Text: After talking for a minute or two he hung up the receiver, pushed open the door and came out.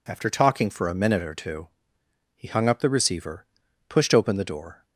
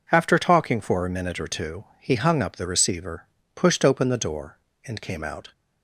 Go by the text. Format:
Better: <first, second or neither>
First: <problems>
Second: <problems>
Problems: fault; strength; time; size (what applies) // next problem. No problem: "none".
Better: second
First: pauses between "two" and "he"; noticeable; at 1.6 s; 0.72 s long // stops before "and came out"; at 4.8 s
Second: none